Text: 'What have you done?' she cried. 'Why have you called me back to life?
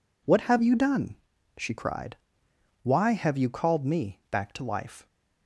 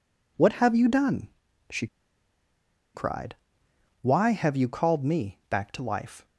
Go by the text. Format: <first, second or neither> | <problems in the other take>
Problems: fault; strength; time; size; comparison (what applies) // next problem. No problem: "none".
first | pauses between "she" and "cried"; at 1.8 s; 1.0 s long